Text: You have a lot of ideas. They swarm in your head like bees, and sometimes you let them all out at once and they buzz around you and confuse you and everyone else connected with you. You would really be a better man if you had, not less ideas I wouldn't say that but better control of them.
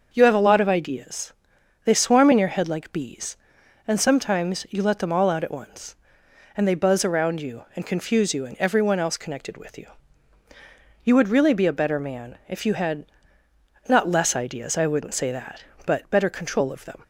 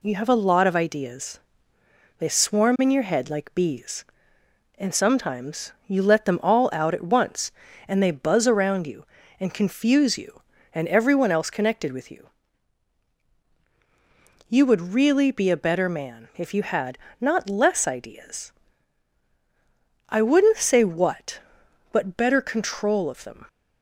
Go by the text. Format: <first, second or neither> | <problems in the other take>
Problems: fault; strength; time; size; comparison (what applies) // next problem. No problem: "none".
first | pauses between "sometimes" and "you"; slight; at 5.7 s; 0.16 s long // pauses between "ideas" and "I"; strong; at 18.5 s; 1.5 s long // says "what" for "that"; at 20.8 s